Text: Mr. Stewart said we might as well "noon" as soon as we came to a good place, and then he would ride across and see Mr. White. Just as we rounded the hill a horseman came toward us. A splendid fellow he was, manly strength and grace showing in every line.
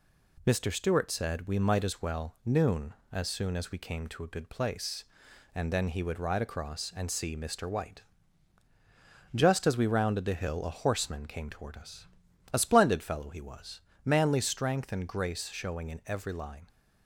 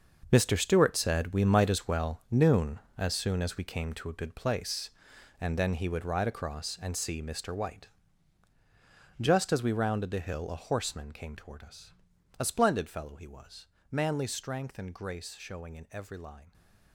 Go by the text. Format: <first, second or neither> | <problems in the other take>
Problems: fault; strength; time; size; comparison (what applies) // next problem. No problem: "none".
first | gets quieter; strong; throughout; 12 dB